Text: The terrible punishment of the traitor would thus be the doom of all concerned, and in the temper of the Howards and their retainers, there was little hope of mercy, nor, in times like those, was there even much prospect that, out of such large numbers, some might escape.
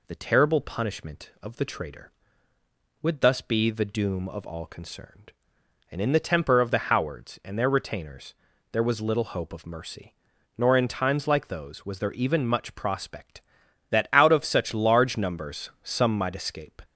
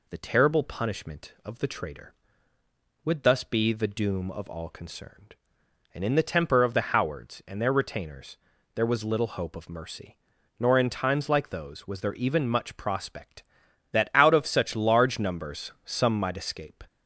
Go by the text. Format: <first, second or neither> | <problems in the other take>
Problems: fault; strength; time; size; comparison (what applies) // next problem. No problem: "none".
neither | none